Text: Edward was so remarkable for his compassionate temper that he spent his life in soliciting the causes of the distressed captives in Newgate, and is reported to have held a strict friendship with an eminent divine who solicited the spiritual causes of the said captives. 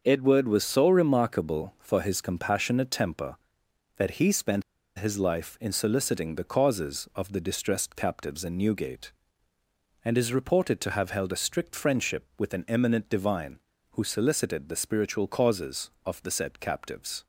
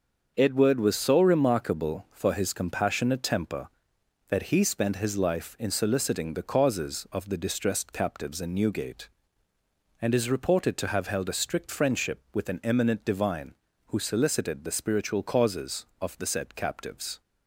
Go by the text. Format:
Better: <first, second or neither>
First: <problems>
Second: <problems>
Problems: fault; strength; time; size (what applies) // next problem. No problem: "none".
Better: second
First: starts louder than the rest; until 1.0 s; 6.5 dB // pauses between "spent" and "his"; slight; at 4.6 s; 0.35 s long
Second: starts louder than the rest; until 1.3 s; 6.5 dB